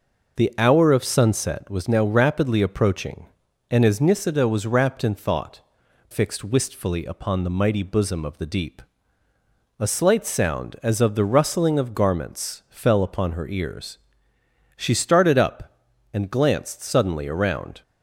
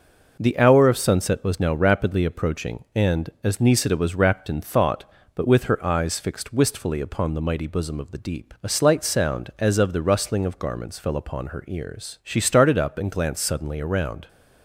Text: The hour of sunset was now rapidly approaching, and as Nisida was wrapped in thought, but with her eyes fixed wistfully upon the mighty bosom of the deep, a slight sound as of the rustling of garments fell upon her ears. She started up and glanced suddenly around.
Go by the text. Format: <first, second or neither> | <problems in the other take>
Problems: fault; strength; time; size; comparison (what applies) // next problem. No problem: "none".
second | skips "but with her eyes"; at 5.8 s